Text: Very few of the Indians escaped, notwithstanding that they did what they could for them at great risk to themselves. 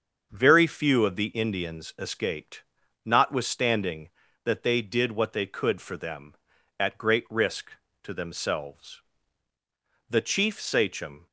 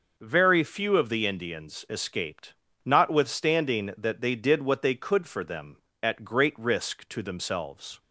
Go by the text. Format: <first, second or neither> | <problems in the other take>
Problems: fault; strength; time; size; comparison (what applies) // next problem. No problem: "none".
second | starts louder than the rest; until 1.3 s; 6.5 dB // goes on to say "The chief Sachem"; noticeable; from 10.0 s on; 1.1 s long